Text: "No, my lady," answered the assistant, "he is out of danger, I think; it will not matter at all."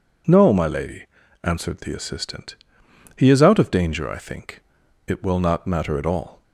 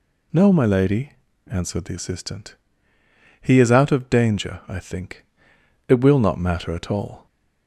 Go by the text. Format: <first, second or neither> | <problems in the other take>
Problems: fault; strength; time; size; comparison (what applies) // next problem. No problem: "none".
neither | none